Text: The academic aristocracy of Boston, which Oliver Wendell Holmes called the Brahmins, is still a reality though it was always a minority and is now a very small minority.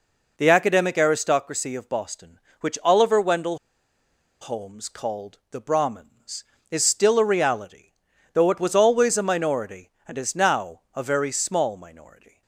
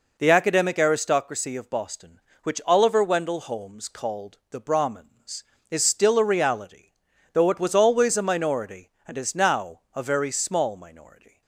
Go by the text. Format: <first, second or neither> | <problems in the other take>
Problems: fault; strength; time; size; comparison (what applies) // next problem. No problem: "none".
second | pauses between "Wendell" and "Holmes"; noticeable; at 3.5 s; 0.83 s long // pauses between "reality" and "though"; noticeable; at 7.8 s; 0.52 s long; noticeable in the second